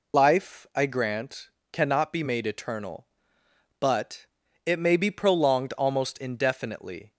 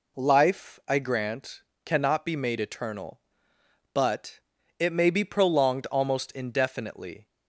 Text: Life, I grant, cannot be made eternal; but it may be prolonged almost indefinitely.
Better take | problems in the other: second | loses the start of "Life"; at 0.1 s; 110 ms // pauses between "but" and "it"; at 4.2 s; 0.40 s long; also in the second

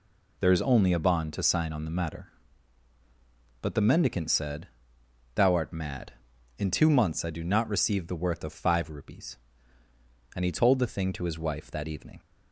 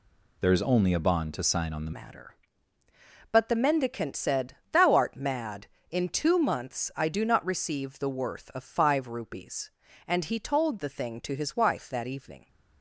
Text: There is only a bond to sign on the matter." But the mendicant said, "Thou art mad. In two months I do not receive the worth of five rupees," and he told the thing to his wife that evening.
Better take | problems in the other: first | changes voice at "matter"; from 1.9 s on; 10.5 s long

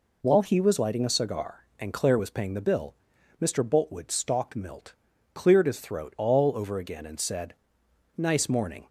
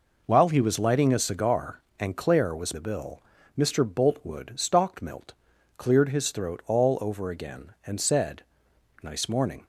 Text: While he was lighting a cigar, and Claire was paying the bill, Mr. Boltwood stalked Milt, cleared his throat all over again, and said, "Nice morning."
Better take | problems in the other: first | skips "paying"; at 2.7 s

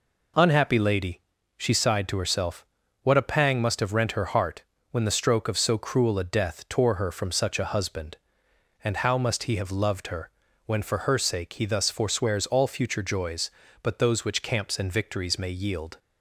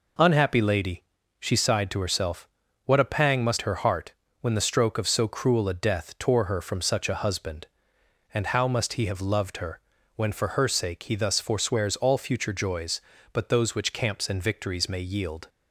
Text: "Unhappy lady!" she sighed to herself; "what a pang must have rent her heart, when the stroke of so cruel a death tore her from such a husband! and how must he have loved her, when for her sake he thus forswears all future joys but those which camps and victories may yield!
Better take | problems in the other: first | skips "have rent"; at 3.6 s

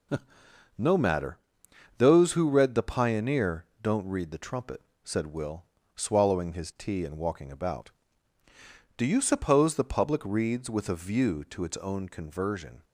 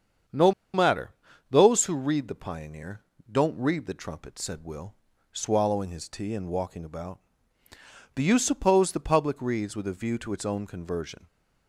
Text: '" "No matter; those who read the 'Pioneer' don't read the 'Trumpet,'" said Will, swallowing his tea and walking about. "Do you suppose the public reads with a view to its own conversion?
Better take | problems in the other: first | starts louder than the rest; strong; until 1.8 s; 7.5 dB // pauses between "No" and "matter"; slight; at 0.5 s; 0.23 s long // pauses between "Pioneer" and "don't"; slight; at 3.0 s; 0.28 s long; slight in the first

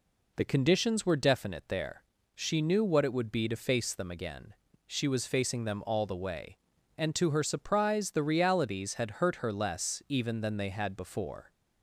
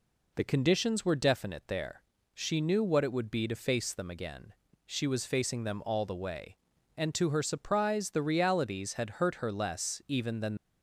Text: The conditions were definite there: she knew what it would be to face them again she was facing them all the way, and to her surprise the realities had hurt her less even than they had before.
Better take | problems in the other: first | pauses between "again" and "she"; at 4.5 s; 0.38 s long; also in the first // stops before "they had before"; at 10.5 s

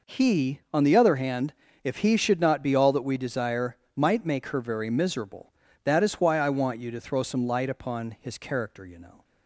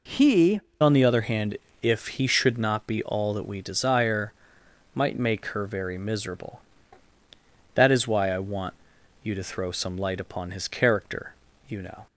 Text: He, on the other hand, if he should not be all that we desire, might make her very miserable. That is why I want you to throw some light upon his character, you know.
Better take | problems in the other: first | changes voice at "on"; from 0.8 s on; 11.2 s long // pauses between "want" and "you"; noticeable; at 8.7 s; 0.48 s long

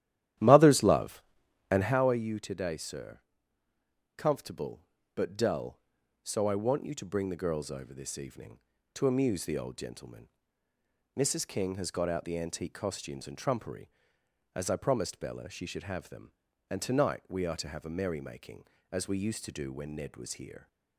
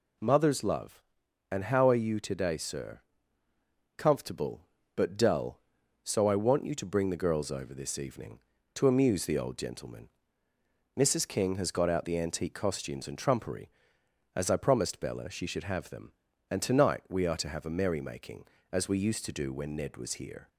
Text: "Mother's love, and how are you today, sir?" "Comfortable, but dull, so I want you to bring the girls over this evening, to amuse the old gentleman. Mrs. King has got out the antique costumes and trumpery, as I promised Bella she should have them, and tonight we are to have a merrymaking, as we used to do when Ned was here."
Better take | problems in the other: second | starts louder than the rest; strong; until 2.0 s; 12.5 dB

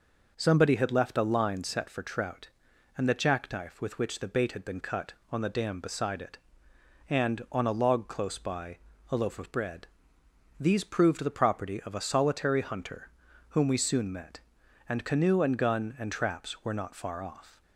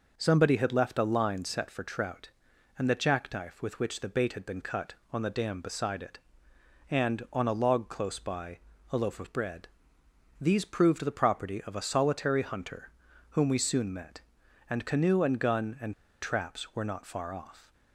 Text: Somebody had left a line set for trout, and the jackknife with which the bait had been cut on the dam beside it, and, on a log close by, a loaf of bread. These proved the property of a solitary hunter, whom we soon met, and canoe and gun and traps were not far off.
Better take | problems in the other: first | pauses between "and" and "traps"; slight; at 15.9 s; 0.28 s long

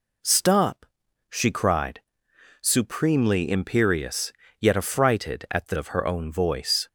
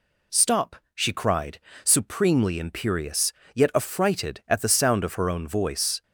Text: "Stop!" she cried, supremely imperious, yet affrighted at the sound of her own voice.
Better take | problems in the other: second | skips "sound"; at 5.7 s

